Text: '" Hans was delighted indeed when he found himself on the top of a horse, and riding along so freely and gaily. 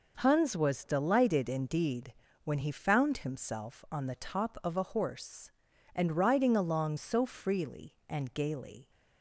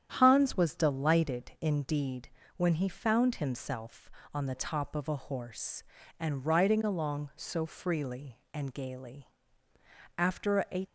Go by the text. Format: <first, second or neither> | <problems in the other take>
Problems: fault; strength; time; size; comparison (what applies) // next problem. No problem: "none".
first | starts louder than the rest; strong; until 1.1 s; 9.5 dB // pauses between "indeed" and "when"; slight; at 2.2 s; 0.28 s long; slight in the first // goes on to say "After a"; noticeable; from 10.1 s on; 0.68 s long